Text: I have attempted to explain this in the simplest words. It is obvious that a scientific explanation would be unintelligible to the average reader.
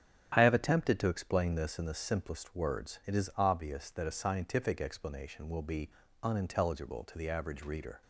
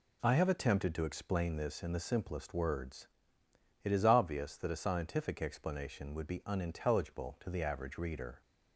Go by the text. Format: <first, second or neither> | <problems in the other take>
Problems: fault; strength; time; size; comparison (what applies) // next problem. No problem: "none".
second | starts louder than the rest; strong; until 1.3 s; 10 dB // says "will" for "would"; at 5.4 s // pauses between "be" and "unintelligible"; slight; at 5.9 s; 0.32 s long